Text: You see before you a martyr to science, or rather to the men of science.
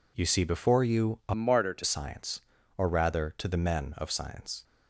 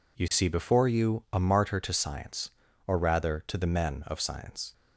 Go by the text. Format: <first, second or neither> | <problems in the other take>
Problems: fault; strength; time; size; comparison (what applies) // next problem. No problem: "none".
second | changes voice from "martyr" to "to"; from 1.3 to 1.8 s; 0.5 s long